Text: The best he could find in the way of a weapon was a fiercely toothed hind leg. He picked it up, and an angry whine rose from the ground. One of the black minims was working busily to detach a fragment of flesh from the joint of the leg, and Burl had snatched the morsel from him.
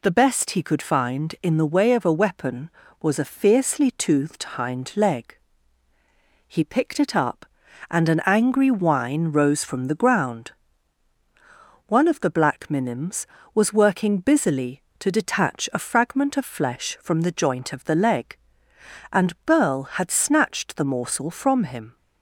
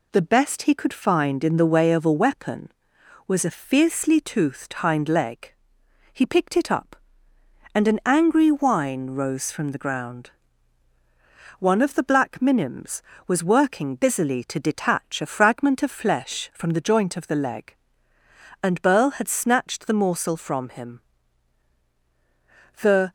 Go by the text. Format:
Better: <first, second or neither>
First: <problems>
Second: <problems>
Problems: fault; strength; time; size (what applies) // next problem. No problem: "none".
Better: first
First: none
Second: goes on to say "The"; slight; from 22.8 s on; 0.30 s long